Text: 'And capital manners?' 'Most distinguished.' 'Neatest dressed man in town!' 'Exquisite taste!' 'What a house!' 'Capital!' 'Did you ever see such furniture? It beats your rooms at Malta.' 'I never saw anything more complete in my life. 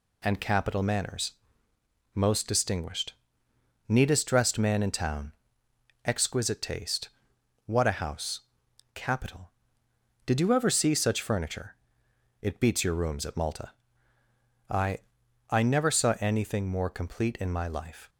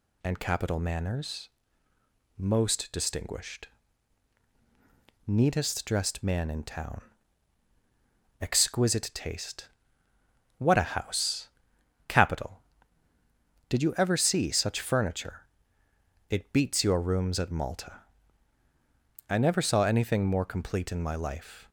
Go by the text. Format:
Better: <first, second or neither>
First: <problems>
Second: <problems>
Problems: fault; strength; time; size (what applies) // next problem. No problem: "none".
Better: second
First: says "I" twice; at 15.4 s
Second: none